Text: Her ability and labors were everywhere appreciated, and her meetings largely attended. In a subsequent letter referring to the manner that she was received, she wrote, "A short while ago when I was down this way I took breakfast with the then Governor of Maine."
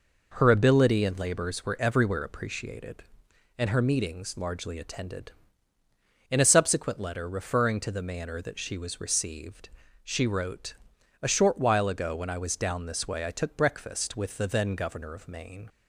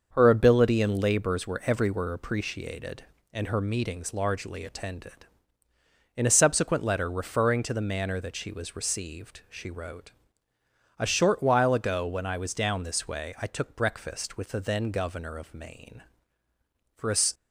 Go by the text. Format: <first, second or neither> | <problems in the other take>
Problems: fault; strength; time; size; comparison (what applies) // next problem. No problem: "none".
first | starts louder than the rest; until 1.1 s; 6.5 dB // goes on to say "For a"; slight; from 16.9 s on; 0.20 s long